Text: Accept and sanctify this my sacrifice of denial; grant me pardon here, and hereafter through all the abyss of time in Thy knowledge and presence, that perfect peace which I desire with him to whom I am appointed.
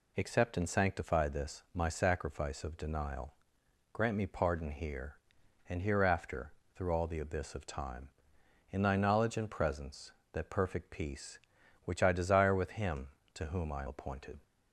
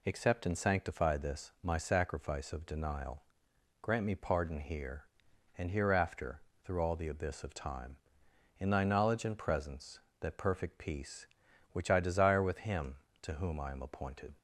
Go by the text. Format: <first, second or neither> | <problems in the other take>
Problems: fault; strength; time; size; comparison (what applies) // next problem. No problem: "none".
second | pauses between "hereafter" and "through"; slight; at 6.5 s; 0.24 s long; slight in the second // skips "am"; at 13.8 s